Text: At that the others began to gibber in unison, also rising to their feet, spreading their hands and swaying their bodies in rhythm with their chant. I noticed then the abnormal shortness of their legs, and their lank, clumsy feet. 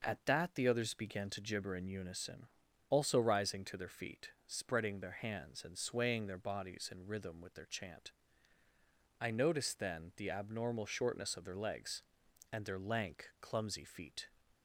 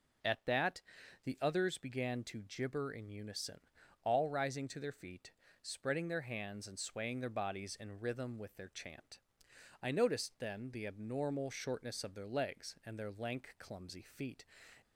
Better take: first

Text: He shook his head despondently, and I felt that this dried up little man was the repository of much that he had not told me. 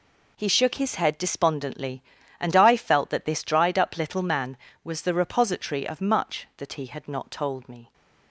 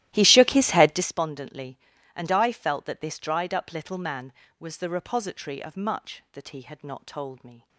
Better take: first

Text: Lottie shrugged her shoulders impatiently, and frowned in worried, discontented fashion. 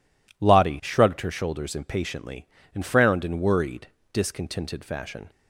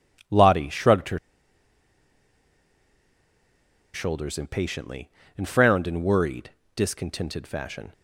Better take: first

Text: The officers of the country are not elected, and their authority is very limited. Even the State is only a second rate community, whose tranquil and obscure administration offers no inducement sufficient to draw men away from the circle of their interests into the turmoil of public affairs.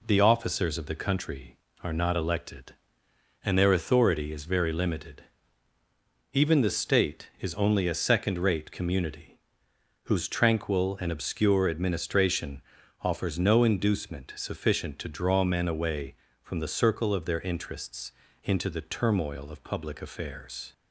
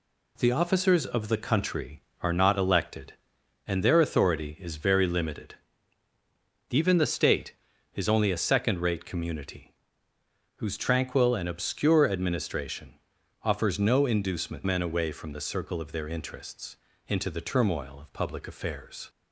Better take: first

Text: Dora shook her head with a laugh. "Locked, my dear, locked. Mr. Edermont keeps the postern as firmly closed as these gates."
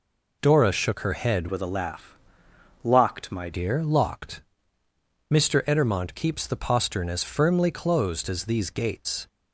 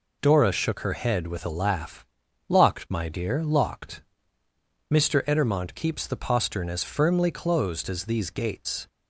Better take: second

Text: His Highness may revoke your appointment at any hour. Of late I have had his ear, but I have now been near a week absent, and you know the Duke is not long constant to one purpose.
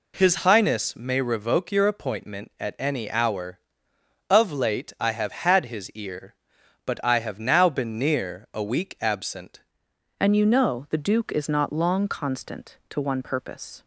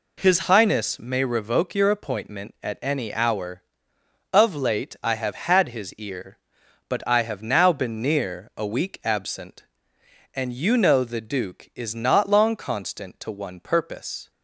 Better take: second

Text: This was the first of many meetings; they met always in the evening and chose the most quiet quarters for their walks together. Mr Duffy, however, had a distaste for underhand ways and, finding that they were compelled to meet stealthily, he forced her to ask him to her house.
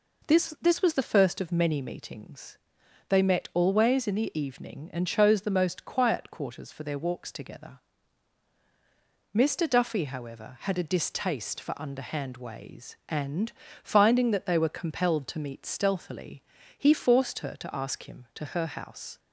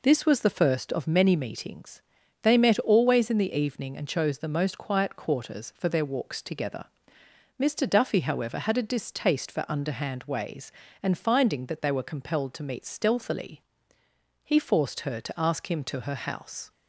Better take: second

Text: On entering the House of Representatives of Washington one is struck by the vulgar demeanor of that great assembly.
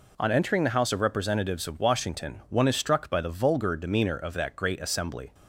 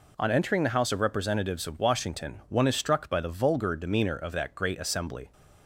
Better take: neither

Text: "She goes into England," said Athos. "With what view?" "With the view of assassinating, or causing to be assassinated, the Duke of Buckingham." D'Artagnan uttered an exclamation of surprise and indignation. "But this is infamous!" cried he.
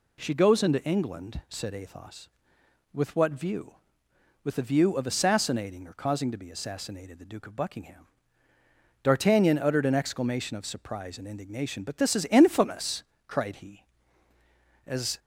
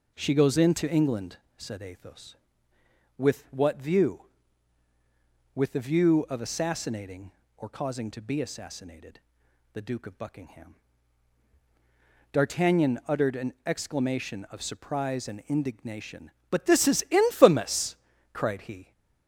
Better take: second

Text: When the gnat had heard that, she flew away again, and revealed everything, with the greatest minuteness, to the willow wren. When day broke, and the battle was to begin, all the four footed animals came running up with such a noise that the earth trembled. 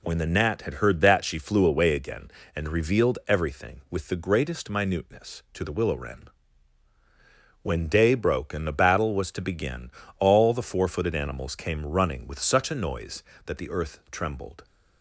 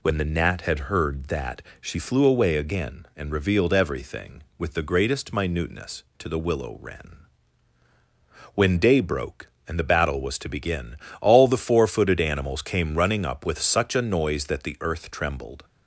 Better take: second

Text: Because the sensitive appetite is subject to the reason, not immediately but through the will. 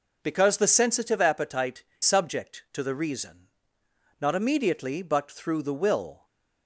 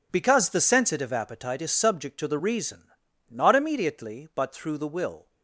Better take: second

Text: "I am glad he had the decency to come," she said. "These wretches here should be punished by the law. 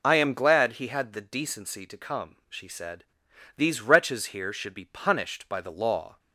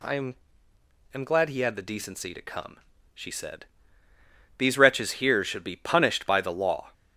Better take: first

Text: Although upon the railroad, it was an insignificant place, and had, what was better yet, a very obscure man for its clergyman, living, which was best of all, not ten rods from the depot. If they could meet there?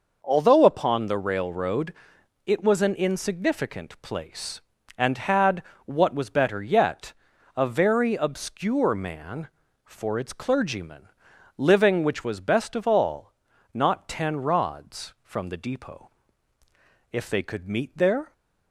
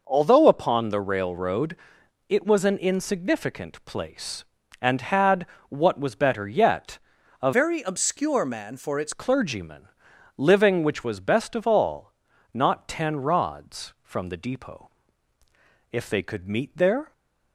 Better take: first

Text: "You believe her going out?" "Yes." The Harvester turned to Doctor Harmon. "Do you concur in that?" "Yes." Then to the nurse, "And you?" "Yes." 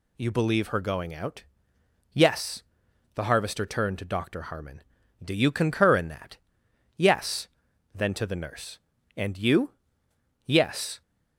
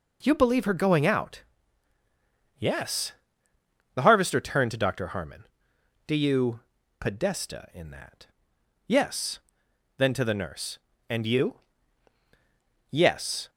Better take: first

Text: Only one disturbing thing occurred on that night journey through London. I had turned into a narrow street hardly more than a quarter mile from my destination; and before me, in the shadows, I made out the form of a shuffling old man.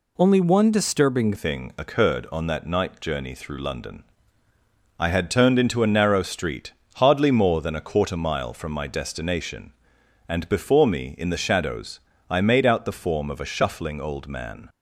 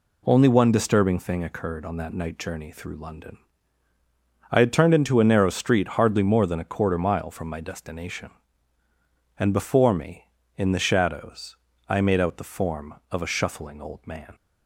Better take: second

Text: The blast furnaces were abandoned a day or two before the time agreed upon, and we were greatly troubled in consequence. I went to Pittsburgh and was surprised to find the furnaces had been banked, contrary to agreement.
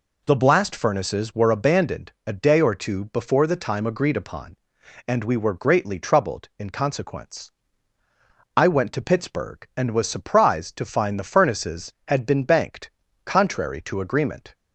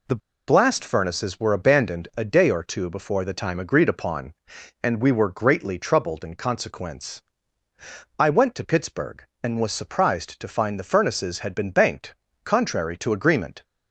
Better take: first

